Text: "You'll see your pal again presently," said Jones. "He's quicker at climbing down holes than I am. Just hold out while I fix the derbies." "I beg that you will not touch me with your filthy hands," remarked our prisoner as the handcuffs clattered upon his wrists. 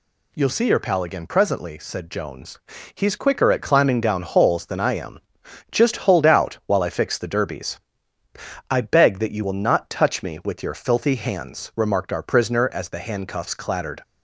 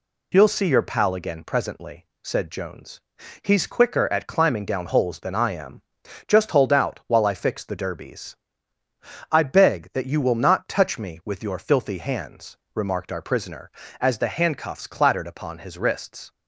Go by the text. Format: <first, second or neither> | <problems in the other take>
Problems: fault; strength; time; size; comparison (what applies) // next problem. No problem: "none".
second | stops before "upon his wrists"; at 14.0 s